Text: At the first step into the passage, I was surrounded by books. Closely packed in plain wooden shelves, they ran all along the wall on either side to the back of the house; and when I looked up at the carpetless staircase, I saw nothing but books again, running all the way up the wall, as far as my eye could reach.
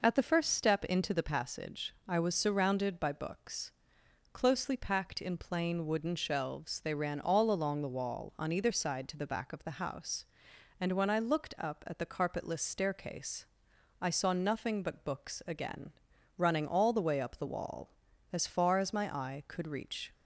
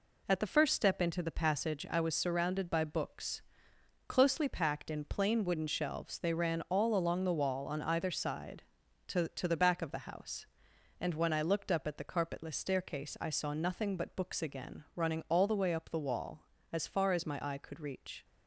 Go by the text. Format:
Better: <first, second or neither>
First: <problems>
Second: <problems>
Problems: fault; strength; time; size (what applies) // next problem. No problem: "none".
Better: first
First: none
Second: says "to" twice; at 9.2 s